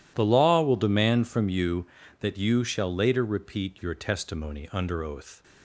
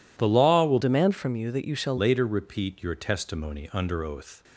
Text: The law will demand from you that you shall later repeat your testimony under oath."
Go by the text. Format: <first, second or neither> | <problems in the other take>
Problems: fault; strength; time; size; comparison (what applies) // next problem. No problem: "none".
first | changes voice from "demand" to "shall"; from 0.8 to 1.9 s; 1.1 s long